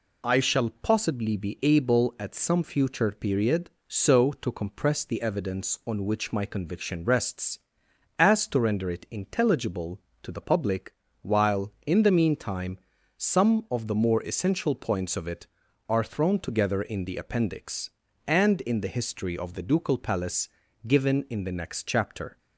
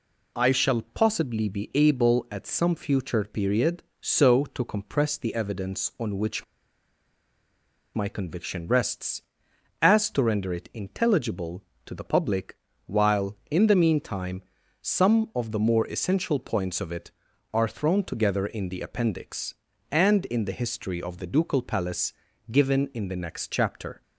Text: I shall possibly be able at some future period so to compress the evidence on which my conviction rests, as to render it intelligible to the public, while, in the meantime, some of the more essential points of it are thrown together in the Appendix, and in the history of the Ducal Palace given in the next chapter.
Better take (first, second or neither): first